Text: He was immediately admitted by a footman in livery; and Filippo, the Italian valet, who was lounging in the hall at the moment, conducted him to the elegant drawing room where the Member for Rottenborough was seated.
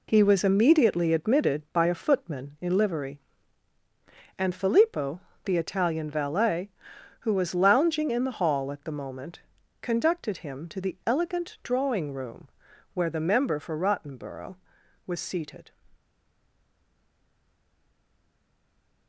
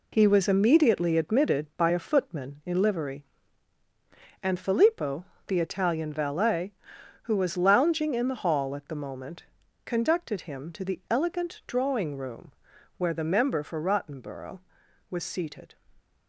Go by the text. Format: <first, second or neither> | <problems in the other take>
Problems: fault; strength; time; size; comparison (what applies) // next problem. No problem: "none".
second | pauses between "room" and "where"; noticeable; at 12.4 s; 0.46 s long; noticeable in the second // stays silent after the last word; strong; from 15.9 s on; 3.1 s long